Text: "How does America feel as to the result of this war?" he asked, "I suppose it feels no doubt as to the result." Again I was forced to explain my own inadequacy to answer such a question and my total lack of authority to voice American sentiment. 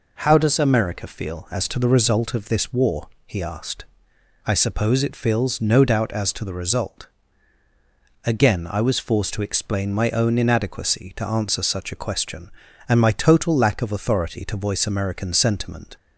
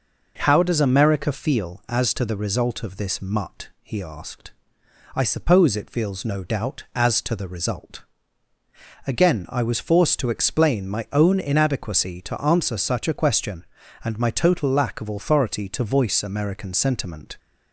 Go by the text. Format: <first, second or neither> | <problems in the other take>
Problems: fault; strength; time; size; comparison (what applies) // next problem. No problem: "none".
first | says "mutt" for "war"; at 3.2 s